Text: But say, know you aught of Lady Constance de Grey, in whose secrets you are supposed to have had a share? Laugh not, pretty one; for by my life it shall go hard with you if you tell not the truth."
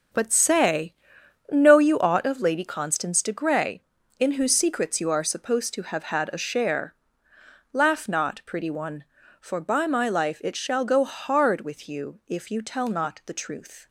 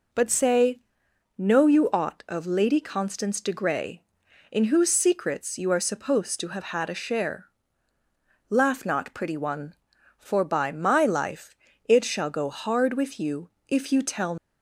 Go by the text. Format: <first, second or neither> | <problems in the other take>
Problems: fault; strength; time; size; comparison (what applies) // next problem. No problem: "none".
first | pauses between "life" and "it"; slight; at 11.5 s; 0.32 s long // pauses between "you" and "if"; slight; at 13.4 s; 0.20 s long // stops before "not the truth"; at 14.3 s